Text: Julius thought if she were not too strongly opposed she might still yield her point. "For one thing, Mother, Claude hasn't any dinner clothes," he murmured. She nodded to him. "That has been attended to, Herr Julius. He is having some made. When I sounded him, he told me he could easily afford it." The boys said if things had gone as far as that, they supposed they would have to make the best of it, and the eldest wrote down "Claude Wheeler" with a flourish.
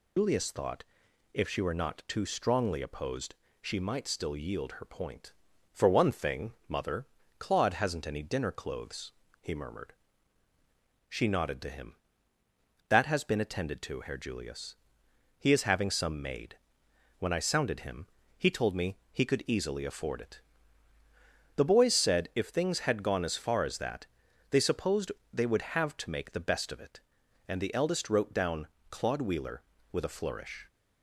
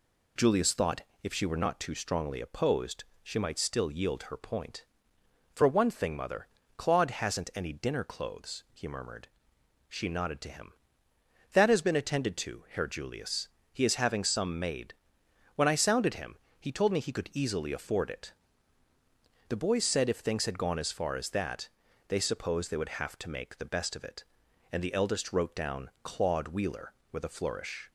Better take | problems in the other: second | loses the start of "Julius"; at 0.1 s; 125 ms // pauses between "thought" and "if"; noticeable; at 0.8 s; 0.48 s long; slight in the second // pauses between "opposed" and "she"; slight; at 3.3 s; 0.26 s long; slight in the second // pauses between "supposed" and "they"; slight; at 25.1 s; 0.22 s long // pauses between "down" and "Claude"; slight; at 28.6 s; 0.24 s long

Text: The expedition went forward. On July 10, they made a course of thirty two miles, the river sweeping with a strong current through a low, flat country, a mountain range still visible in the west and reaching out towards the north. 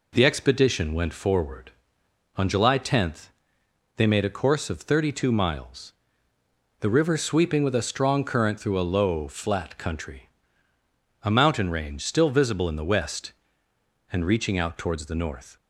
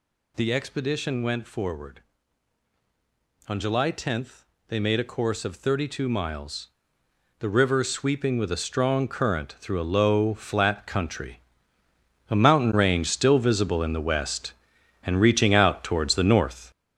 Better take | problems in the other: first | gets louder; strong; throughout; 8 dB

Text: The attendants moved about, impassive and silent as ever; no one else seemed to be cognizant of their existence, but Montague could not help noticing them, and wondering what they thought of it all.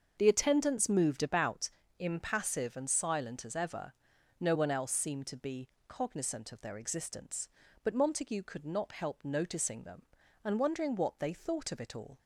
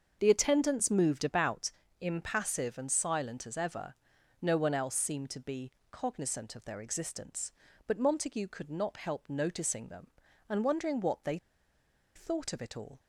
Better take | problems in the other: first | starts louder than the rest; until 1.2 s; 6.5 dB; also in the first // pauses between "be" and "cognizant"; slight; at 5.7 s; 0.18 s long; slight in the first // pauses between "they" and "thought"; noticeable; at 11.3 s; 0.78 s long

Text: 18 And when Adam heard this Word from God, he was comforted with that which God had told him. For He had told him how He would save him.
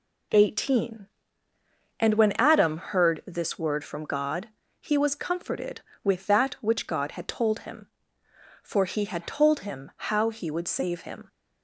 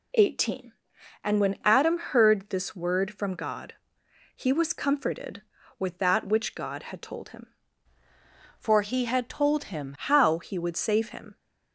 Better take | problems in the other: first | changes voice from "For" to "him"; from 8.5 to 9.9 s; 1.4 s long

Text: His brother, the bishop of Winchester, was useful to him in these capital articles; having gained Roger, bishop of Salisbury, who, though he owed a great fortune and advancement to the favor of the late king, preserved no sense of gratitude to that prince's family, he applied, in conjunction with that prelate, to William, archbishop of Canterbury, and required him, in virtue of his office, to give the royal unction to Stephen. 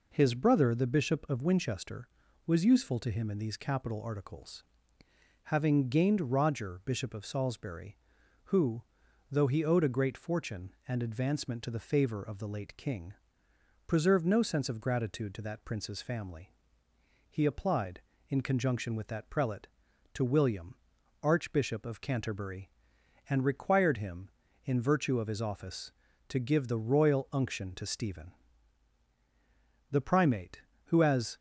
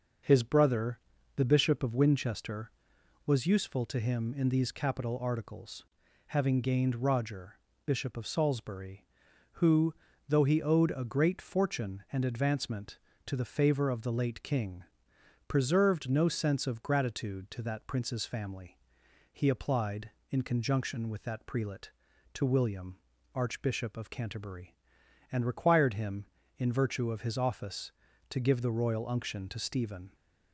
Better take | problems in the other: second | goes on to say "The primate who as"; from 29.9 s on; 1.4 s long

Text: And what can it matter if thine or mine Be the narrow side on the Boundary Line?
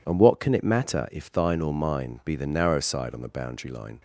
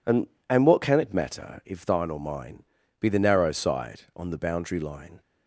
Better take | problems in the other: first | says "And" twice; at 0.4 s // pauses between "mine" and "Be"; slight; at 2.6 s; 0.36 s long

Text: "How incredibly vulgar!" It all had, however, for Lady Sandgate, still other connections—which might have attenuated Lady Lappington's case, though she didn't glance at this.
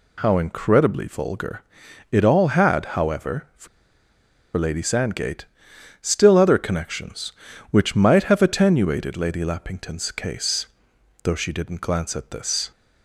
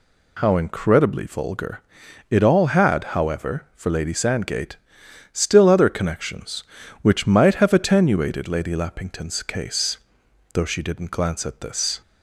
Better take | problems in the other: second | pauses between "for" and "Lady"; noticeable; at 3.6 s; 0.89 s long

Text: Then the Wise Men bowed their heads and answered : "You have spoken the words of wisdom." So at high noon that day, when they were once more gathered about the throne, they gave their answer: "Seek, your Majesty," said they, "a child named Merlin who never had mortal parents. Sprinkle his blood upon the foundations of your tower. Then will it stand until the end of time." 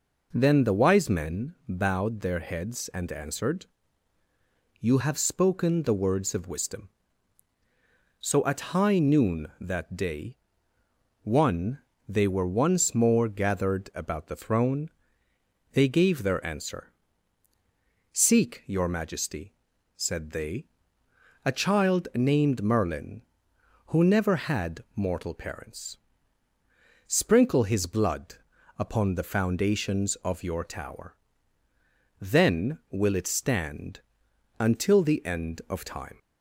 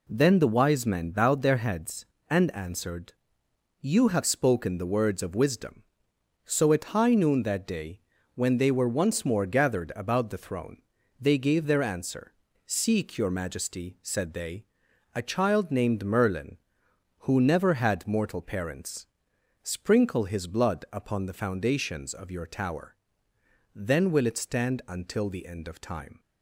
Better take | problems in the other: second | says "one" for "when"; at 11.2 s // pauses between "blood" and "upon"; at 28.3 s; 0.42 s long // pauses between "stand" and "until"; noticeable; at 33.9 s; 0.58 s long

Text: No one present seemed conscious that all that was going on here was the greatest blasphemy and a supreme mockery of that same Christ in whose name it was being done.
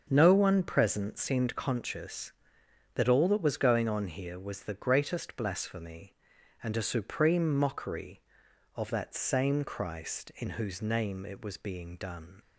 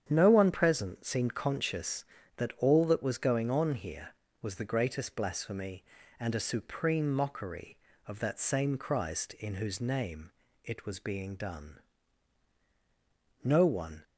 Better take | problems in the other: first | starts louder than the rest; strong; until 1.1 s; 8.5 dB; also in the first // pauses between "name" and "it"; slight; at 10.3 s; 0.32 s long // goes on to say "No one"; from 13.4 s on; 0.60 s long

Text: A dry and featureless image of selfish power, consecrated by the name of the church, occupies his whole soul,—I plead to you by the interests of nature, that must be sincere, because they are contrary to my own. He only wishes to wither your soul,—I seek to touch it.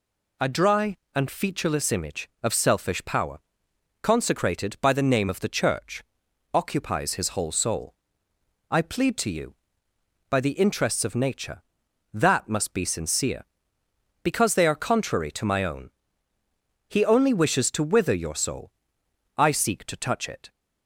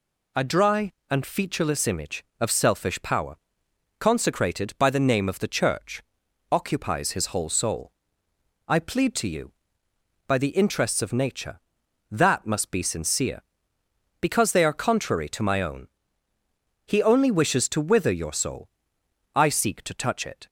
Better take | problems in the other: neither | none

